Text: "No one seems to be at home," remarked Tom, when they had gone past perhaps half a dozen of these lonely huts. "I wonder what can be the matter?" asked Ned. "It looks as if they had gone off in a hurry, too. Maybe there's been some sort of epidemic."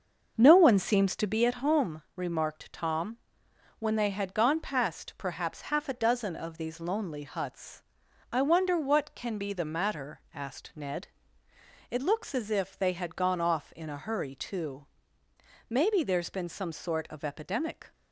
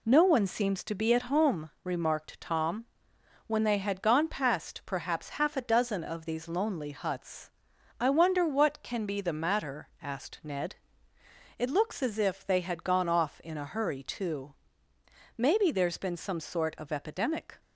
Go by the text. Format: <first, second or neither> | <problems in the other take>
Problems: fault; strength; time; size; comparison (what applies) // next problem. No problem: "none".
second | starts louder than the rest; until 1.4 s; 6 dB